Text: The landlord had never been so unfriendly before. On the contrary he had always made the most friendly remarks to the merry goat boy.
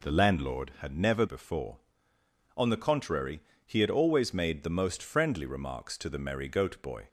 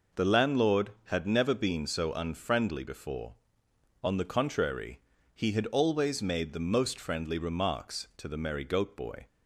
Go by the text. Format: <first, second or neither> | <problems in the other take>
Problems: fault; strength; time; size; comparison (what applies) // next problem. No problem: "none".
second | skips "been so unfriendly"; at 1.2 s // pauses between "contrary" and "he"; slight; at 3.3 s; 0.26 s long; slight in the second